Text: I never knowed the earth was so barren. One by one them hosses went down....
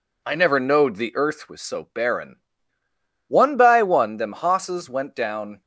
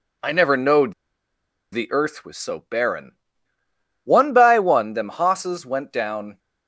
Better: first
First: none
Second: pauses between "knowed" and "the"; noticeable; at 0.9 s; 0.78 s long

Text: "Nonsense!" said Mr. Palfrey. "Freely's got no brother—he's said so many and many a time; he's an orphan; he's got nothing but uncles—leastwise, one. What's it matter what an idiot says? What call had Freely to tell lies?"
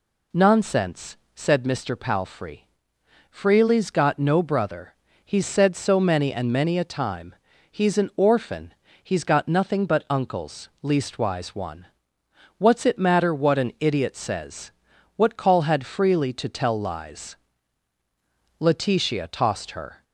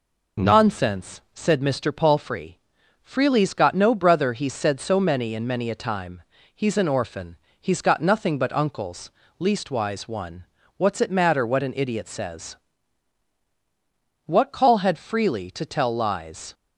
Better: second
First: goes on to say "Letitia tossed her"; from 18.5 s on; 1.4 s long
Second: none

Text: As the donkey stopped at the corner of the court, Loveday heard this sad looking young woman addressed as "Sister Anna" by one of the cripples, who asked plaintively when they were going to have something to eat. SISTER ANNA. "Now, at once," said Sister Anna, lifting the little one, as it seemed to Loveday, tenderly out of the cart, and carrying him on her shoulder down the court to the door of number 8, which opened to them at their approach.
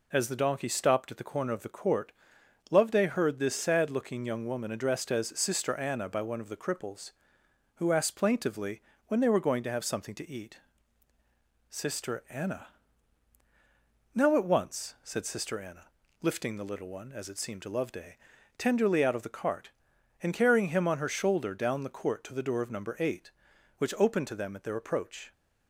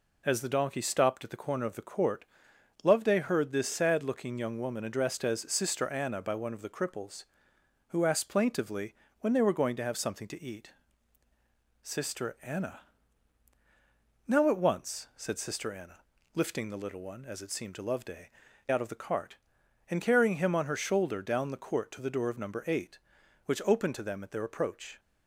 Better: first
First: pauses between "plaintively" and "when"; slight; at 8.8 s; 0.26 s long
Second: pauses between "plaintively" and "when"; slight; at 8.9 s; 0.26 s long // skips "tenderly"; at 18.4 s

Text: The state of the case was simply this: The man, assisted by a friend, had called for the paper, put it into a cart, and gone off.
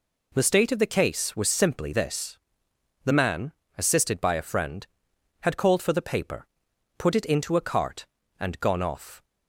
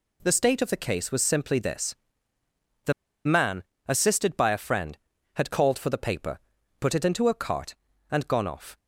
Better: first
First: none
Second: pauses between "The" and "man"; slight; at 2.9 s; 0.32 s long

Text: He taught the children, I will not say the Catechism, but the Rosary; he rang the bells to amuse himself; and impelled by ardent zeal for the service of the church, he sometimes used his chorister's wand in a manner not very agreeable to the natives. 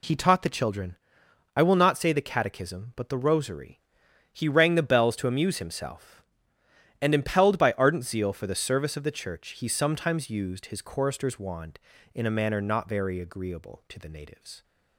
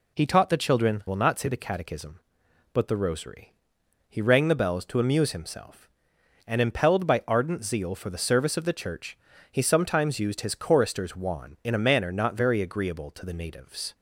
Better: first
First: none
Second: skips "I"; at 1.0 s

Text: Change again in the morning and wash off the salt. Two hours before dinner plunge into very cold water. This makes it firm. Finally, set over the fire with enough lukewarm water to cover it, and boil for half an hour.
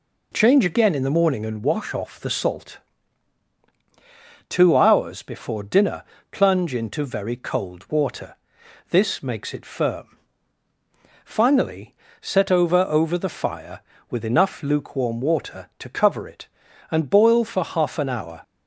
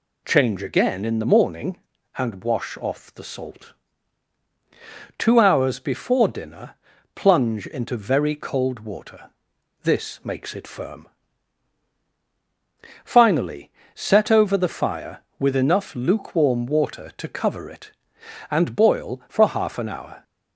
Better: second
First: pauses between "dinner" and "plunge"; slight; at 6.0 s; 0.28 s long // says "over" twice; at 12.8 s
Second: pauses between "dinner" and "plunge"; at 6.7 s; 0.38 s long

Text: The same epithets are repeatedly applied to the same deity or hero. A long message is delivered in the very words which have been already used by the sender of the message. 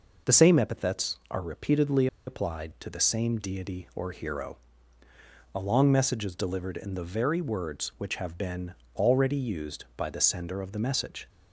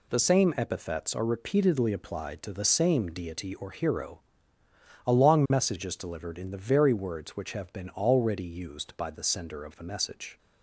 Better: second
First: pauses between "repeatedly" and "applied"; slight; at 2.0 s; 0.20 s long // pauses between "been" and "already"; slight; at 8.7 s; 0.20 s long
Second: none

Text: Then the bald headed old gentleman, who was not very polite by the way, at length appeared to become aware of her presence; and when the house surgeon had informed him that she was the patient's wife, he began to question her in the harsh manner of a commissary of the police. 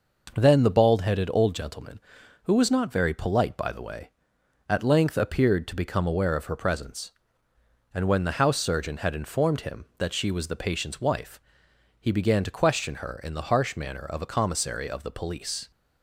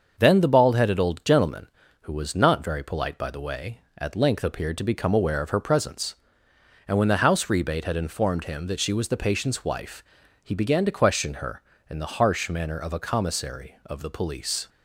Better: first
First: none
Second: starts louder than the rest; until 1.1 s; 6.5 dB // says "rebate" for "surgeon"; at 7.4 s

